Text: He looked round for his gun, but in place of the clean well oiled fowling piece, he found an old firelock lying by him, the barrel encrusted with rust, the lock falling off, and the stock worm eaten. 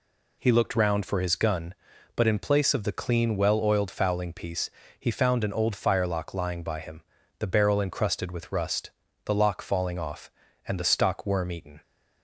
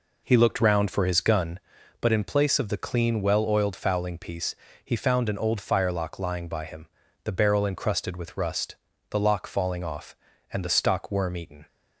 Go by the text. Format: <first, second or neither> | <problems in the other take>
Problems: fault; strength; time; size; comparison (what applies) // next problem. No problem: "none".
first | starts louder than the rest; noticeable; until 1.8 s; 4 dB